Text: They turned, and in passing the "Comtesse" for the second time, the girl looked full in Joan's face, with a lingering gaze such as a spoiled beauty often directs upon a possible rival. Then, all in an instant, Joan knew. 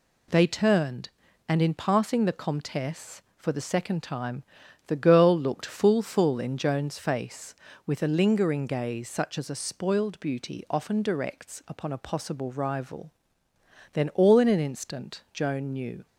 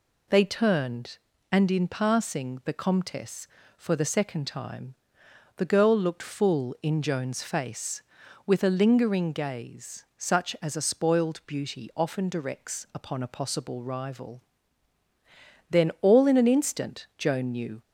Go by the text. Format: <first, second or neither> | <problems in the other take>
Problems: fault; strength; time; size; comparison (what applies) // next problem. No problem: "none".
second | says "full" twice; at 6.0 s